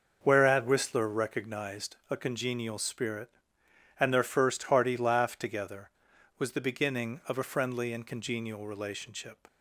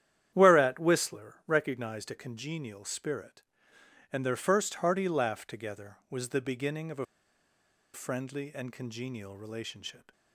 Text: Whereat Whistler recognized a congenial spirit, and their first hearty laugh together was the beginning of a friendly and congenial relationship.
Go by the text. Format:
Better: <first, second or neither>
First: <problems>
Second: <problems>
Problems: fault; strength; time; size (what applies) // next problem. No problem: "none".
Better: first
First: starts louder than the rest; noticeable; until 1.2 s; 6 dB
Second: starts louder than the rest; strong; until 1.3 s; 10.5 dB // pauses between "a" and "friendly"; noticeable; at 7.0 s; 0.88 s long